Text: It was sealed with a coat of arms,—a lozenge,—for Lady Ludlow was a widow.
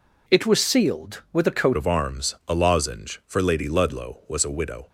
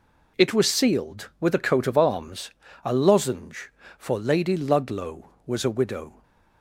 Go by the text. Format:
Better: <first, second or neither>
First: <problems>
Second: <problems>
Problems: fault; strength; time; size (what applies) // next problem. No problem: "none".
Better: second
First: changes voice at "of"; from 1.7 s on; 3.1 s long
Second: none